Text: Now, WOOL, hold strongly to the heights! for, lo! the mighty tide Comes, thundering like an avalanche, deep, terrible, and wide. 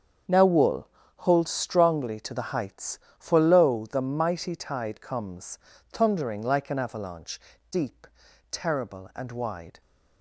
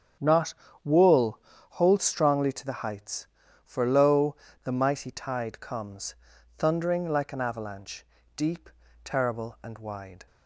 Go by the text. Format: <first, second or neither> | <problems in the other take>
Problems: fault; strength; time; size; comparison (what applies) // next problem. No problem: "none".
first | starts louder than the rest; strong; until 1.8 s; 7.5 dB; strong in the first // says "Not" for "Now"; at 0.1 s